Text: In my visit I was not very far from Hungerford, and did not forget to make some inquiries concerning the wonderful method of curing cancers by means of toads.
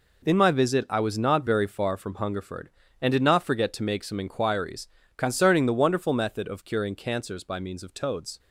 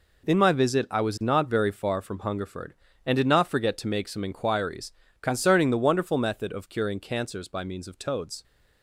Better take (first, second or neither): neither